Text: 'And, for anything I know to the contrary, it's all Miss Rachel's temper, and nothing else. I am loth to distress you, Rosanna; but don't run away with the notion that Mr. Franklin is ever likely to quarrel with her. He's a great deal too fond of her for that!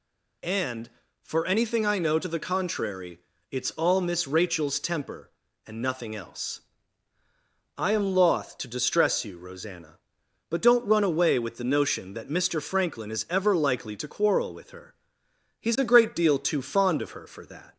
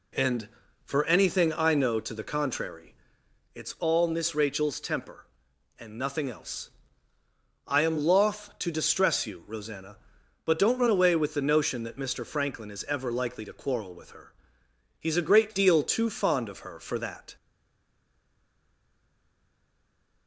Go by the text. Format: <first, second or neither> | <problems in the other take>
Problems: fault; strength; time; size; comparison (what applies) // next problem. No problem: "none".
first | stays silent after the last word; strong; from 17.3 s on; 2.9 s long